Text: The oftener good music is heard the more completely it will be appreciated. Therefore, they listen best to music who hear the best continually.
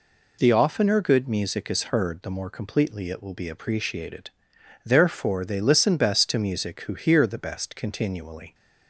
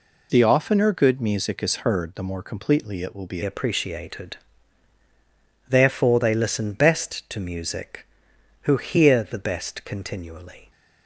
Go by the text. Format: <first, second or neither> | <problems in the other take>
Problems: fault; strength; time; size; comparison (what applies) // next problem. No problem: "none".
first | changes voice at "appreciated"; from 3.4 s on; 7.2 s long